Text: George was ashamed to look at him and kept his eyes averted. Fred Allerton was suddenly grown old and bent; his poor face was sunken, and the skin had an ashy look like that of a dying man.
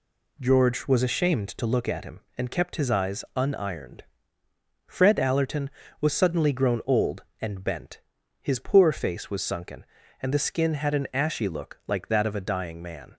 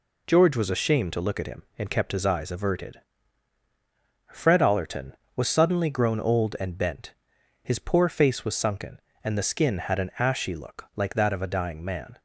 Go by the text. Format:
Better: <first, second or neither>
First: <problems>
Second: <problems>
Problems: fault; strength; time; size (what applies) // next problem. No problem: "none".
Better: second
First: says "unironed" for "averted"; at 3.3 s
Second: none